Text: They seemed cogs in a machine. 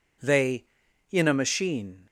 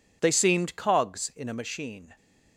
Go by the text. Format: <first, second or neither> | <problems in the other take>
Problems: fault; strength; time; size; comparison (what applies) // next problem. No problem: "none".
second | skips "seemed cogs"; at 0.8 s